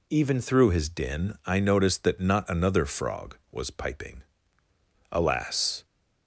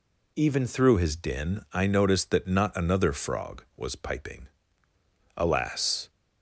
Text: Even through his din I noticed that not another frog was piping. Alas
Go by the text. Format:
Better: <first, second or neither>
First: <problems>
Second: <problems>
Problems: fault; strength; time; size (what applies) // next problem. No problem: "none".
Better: neither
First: none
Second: none